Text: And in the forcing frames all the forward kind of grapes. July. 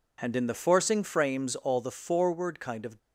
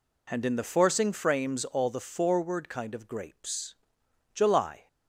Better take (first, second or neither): second